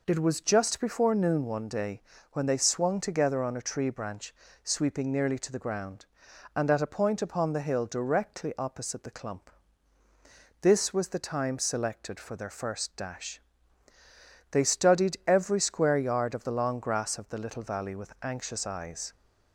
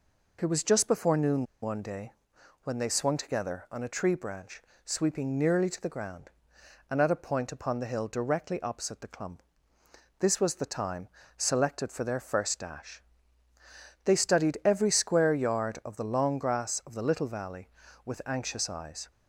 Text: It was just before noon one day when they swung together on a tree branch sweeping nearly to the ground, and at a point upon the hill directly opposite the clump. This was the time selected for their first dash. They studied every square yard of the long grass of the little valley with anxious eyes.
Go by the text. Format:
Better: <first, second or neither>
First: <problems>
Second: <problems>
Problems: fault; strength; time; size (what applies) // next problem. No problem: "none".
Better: first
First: pauses between "day" and "when"; slight; at 2.0 s; 0.30 s long // pauses between "branch" and "sweeping"; slight; at 4.3 s; 0.30 s long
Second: pauses between "noon" and "one"; slight; at 1.4 s; 0.18 s long // pauses between "day" and "when"; noticeable; at 2.1 s; 0.52 s long // pauses between "branch" and "sweeping"; slight; at 4.6 s; 0.24 s long // pauses between "time" and "selected"; slight; at 11.0 s; 0.28 s long